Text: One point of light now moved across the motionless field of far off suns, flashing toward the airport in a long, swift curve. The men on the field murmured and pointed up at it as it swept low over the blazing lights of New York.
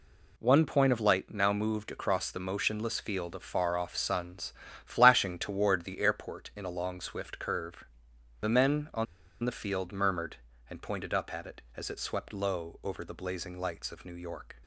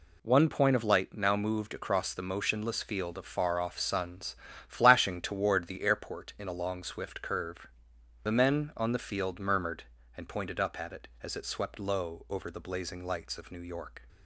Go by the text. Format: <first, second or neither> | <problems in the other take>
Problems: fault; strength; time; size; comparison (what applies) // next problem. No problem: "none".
second | pauses between "on" and "the"; at 9.0 s; 0.38 s long